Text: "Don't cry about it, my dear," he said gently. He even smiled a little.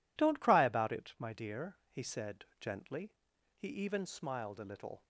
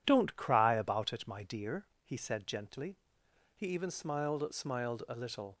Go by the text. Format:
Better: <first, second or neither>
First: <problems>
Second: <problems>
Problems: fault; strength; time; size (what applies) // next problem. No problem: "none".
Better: first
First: none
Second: says "smiled" twice; at 4.5 s